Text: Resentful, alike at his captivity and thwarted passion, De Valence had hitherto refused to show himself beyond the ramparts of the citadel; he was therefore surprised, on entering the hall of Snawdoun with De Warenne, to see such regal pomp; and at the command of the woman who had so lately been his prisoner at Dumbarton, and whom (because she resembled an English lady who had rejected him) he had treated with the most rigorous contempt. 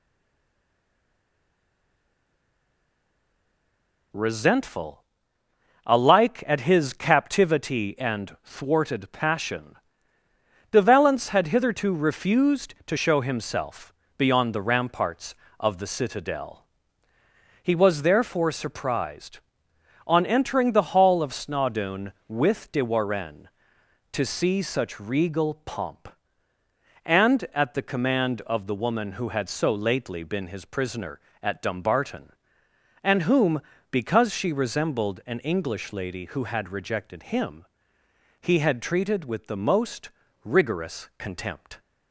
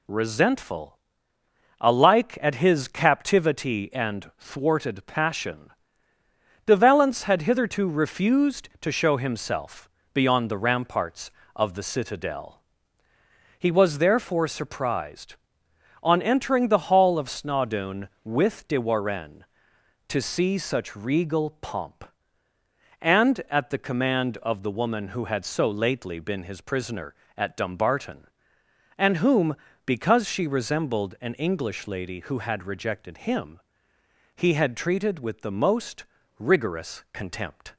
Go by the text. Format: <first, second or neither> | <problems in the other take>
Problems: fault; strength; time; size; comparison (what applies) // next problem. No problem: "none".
second | stays silent before the first word; strong; until 4.1 s; 4.1 s long // pauses between "himself" and "beyond"; slight; at 13.9 s; 0.24 s long; slight in the second // pauses between "most" and "rigorous"; slight; at 40.0 s; 0.34 s long; slight in the second